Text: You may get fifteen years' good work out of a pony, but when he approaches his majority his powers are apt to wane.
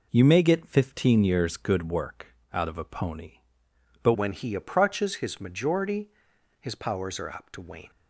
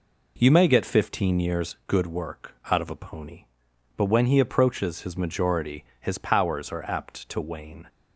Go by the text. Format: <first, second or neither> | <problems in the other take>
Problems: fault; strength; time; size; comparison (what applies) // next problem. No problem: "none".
second | pauses between "work" and "out"; slight; at 2.3 s; 0.18 s long; slight in the second // changes voice at "when"; from 4.1 s on; 3.8 s long // pauses between "majority" and "his"; noticeable; at 6.0 s; 0.52 s long; slight in the second